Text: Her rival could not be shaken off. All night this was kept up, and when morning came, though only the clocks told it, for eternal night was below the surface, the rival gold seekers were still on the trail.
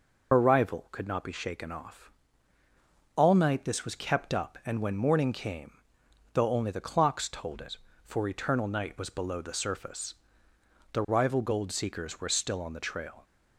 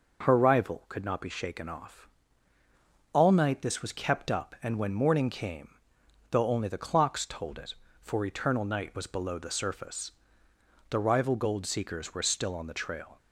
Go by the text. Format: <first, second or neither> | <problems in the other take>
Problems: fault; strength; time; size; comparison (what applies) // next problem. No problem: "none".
second | loses the start of "Her"; at 0.3 s; 80 ms